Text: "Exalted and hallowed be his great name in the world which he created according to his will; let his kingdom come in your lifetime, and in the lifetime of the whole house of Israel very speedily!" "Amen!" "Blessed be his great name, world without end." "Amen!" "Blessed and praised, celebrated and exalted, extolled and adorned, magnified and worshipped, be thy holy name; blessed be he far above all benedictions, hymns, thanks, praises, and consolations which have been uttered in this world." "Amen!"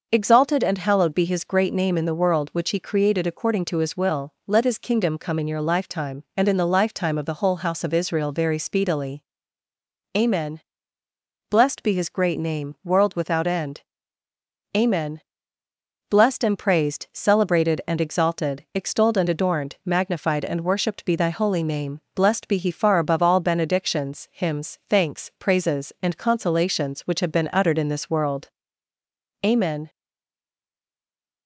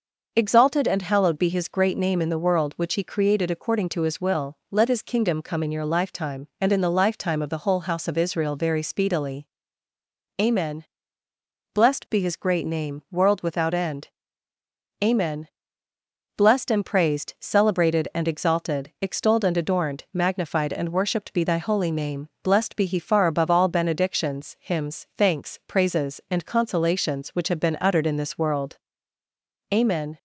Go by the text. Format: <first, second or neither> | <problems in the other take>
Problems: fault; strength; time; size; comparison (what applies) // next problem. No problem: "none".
second | starts louder than the rest; noticeable; until 1.1 s; 6 dB; noticeable in the second // stays silent after the last word; noticeable; from 29.8 s on; 1.6 s long